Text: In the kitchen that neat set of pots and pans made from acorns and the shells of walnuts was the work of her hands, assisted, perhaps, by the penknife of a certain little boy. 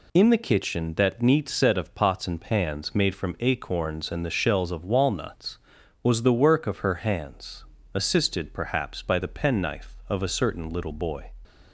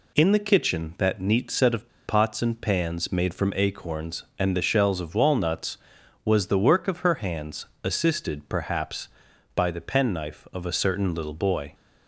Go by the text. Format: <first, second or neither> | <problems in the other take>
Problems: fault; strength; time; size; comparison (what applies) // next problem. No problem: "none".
first | pauses between "of" and "pots"; slight; at 1.8 s; 0.17 s long